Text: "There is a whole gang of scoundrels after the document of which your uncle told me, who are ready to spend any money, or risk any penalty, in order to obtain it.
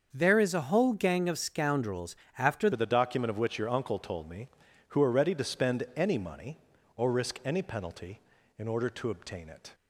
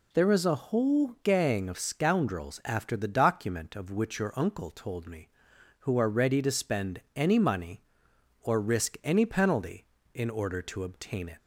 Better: second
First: starts louder than the rest; until 1.1 s; 6.5 dB // pauses between "scoundrels" and "after"; slight; at 2.1 s; 0.22 s long // changes voice at "the"; from 2.7 s on; 7.0 s long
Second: none

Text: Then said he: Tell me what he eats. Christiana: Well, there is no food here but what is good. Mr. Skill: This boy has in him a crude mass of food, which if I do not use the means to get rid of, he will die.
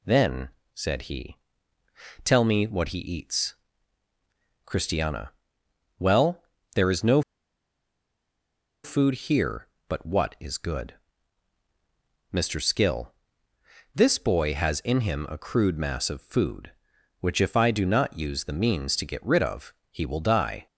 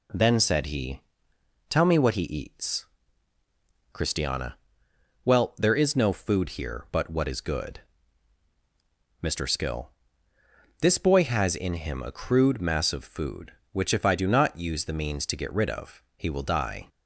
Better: second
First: pauses between "Then" and "said"; slight; at 0.4 s; 0.26 s long // pauses between "no" and "food"; strong; at 7.2 s; 1.6 s long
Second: none

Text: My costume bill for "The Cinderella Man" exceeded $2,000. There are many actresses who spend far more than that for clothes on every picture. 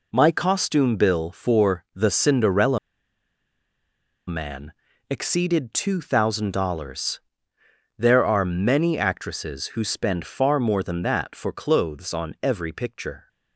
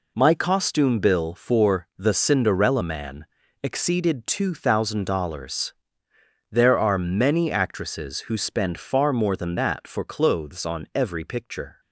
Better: second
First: pauses between "Cinderella" and "Man"; strong; at 2.7 s; 1.4 s long // pauses between "Man" and "exceeded"; slight; at 4.7 s; 0.36 s long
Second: pauses between "Man" and "exceeded"; slight; at 3.2 s; 0.36 s long

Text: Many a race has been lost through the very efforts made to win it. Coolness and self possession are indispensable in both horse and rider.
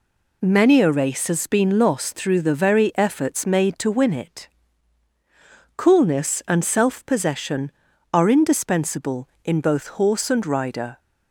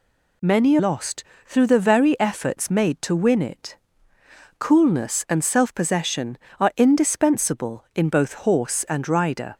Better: first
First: none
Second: skips "a race has been"; at 0.7 s // pauses between "lost" and "through"; slight; at 1.2 s; 0.22 s long

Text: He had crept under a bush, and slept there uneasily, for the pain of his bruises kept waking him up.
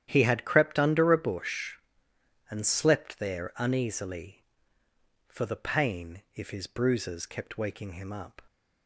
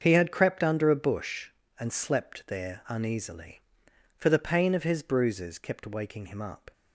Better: second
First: starts louder than the rest; strong; until 1.0 s; 10.5 dB // says "if" for "of"; at 6.3 s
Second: starts louder than the rest; until 1.0 s; 7 dB

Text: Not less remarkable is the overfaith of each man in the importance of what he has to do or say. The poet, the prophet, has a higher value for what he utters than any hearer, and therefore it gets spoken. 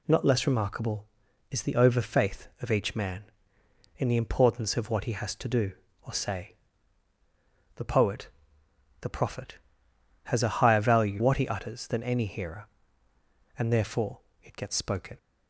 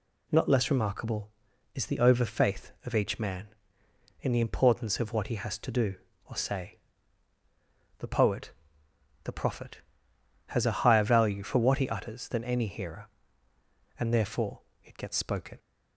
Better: second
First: skips "for"; at 11.2 s // pauses between "therefore" and "it"; slight; at 14.2 s; 0.20 s long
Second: pauses between "therefore" and "it"; slight; at 14.6 s; 0.20 s long

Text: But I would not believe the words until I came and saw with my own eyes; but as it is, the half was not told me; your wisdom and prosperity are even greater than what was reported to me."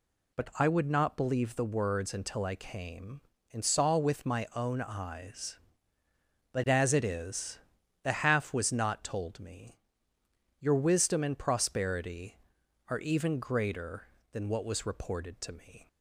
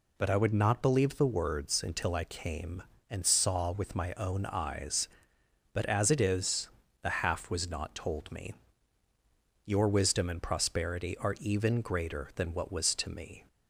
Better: first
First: none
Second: skips "reported"; at 12.9 s

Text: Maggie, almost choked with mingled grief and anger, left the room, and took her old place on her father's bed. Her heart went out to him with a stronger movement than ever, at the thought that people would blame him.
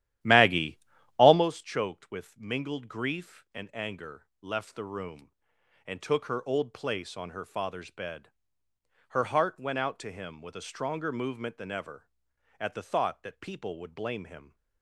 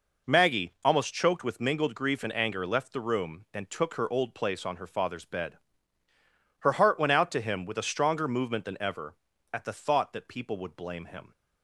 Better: second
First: starts louder than the rest; strong; until 1.5 s; 12.5 dB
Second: none

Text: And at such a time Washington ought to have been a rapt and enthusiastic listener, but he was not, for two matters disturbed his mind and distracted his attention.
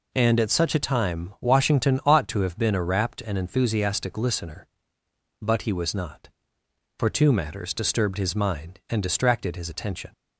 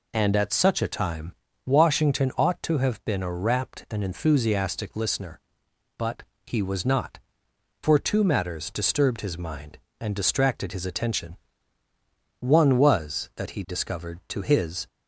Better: first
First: none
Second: pauses between "time" and "Washington"; slight; at 1.3 s; 0.32 s long // pauses between "but" and "he"; slight; at 6.2 s; 0.20 s long // goes on to say "One was that he discovered to his"; strong; from 12.4 s on; 2.4 s long

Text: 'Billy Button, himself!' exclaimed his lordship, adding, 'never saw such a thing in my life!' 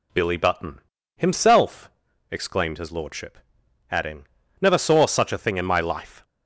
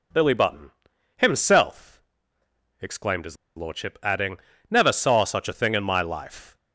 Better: first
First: none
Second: pauses between "his" and "lordship"; slight; at 3.3 s; 0.20 s long

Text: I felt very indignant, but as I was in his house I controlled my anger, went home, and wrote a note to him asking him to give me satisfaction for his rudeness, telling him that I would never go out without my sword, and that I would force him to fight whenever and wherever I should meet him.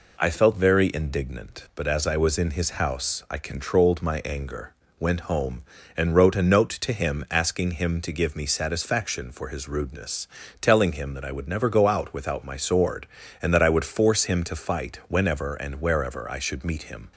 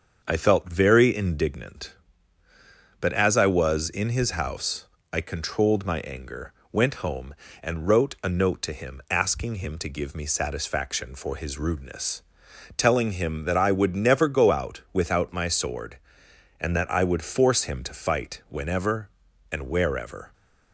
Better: first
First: none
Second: starts louder than the rest; until 1.2 s; 7 dB // pauses between "house" and "I"; slight; at 4.8 s; 0.26 s long // stops before "I should meet him"; at 20.3 s

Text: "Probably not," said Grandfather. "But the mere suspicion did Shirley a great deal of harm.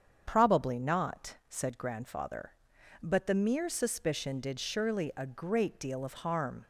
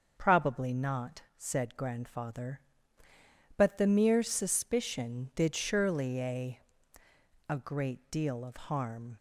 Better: first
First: starts louder than the rest; strong; until 1.2 s; 7.5 dB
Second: starts louder than the rest; until 1.1 s; 6.5 dB // says "a" twice; at 7.4 s

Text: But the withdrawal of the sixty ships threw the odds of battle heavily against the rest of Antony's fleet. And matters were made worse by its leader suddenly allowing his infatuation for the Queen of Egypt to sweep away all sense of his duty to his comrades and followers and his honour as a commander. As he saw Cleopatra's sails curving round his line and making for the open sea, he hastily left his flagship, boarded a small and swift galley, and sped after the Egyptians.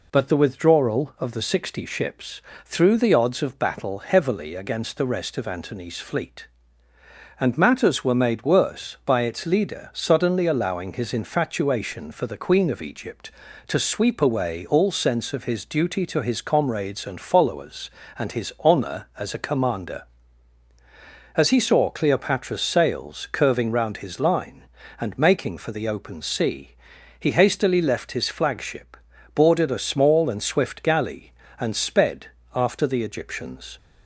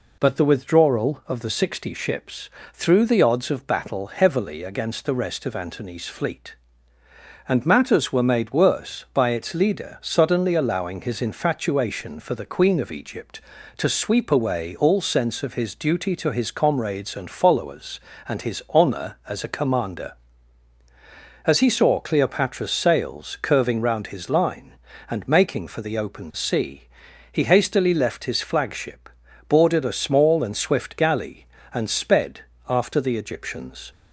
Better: neither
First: pauses between "ships" and "threw"; slight; at 2.4 s; 0.24 s long // pauses between "sped" and "after"; slight; at 32.2 s; 0.28 s long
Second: pauses between "ships" and "threw"; slight; at 2.4 s; 0.24 s long // pauses between "sped" and "after"; slight; at 32.4 s; 0.28 s long

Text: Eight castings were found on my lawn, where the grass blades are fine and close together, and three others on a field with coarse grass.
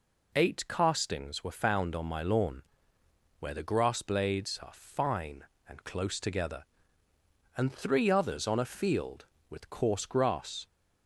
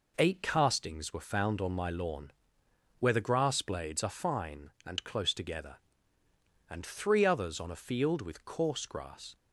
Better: neither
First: none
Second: none

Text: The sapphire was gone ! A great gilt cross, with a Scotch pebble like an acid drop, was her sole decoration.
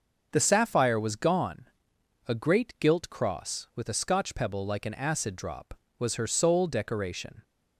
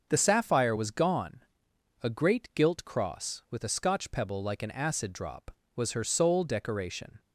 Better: neither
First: starts louder than the rest; until 1.3 s; 6.5 dB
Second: starts louder than the rest; until 1.1 s; 6.5 dB

